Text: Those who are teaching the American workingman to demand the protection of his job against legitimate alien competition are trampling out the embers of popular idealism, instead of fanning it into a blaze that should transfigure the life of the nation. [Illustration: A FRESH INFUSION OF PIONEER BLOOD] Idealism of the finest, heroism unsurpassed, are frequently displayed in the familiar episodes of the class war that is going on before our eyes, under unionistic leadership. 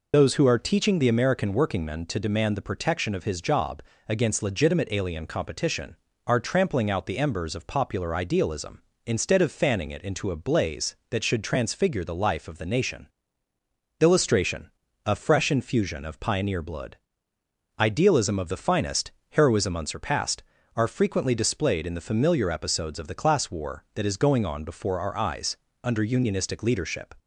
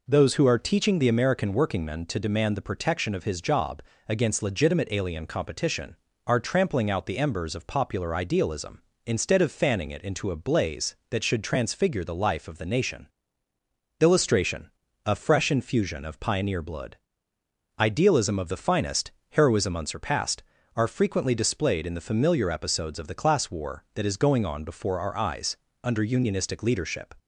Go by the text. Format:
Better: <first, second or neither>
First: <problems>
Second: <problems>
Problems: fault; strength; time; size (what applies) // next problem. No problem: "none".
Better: second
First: loses the start of "Those"; at 0.1 s; 55 ms // pauses between "job" and "against"; slight; at 3.8 s; 0.26 s long // pauses between "BLOOD" and "Idealism"; noticeable; at 16.9 s; 0.82 s long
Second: pauses between "job" and "against"; slight; at 3.8 s; 0.26 s long // pauses between "BLOOD" and "Idealism"; noticeable; at 16.9 s; 0.82 s long